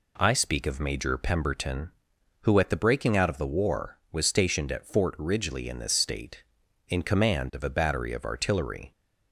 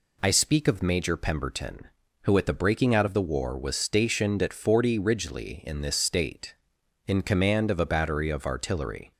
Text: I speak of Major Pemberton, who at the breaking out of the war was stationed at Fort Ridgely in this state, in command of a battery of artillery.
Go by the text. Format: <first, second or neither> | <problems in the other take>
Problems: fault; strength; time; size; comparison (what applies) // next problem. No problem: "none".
first | says "Forty" for "Fort"; at 4.5 s